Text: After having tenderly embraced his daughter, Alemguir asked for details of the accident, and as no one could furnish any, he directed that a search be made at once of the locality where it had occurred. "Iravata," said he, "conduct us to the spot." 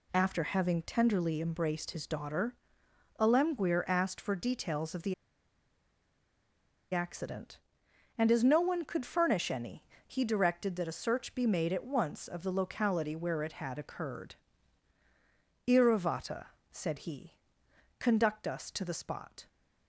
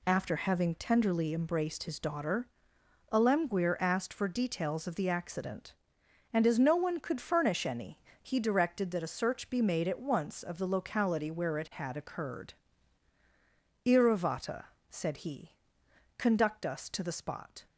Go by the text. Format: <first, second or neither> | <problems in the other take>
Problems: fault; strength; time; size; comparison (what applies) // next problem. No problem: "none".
second | pauses between "the" and "accident"; strong; at 5.1 s; 1.7 s long